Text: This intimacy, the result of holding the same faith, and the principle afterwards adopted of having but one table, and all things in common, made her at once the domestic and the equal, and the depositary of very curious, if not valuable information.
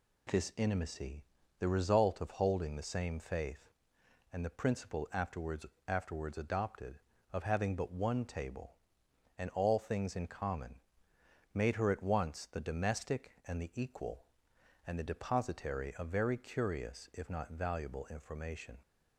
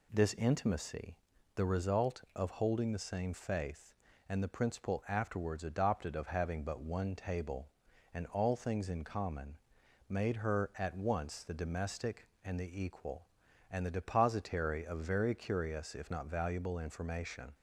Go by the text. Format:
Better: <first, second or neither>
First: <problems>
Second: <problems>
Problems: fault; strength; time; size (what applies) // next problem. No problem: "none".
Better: second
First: says "afterwards" twice; at 5.8 s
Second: none